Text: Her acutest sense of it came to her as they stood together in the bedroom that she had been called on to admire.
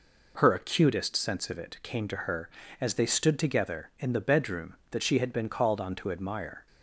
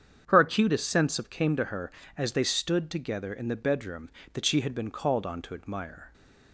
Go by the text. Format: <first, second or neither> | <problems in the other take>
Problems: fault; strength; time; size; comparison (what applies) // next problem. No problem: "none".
first | starts louder than the rest; strong; until 1.2 s; 8 dB // skips "it"; at 1.2 s